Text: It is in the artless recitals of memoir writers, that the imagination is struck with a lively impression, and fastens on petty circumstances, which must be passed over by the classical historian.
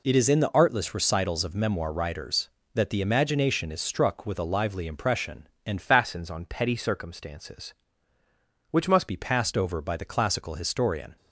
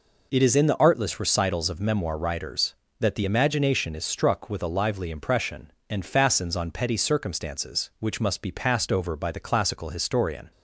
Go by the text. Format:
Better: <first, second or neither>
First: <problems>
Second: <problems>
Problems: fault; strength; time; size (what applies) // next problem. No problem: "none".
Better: second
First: changes voice from "fastens" to "must"; from 5.8 to 9.0 s; 3.2 s long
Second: none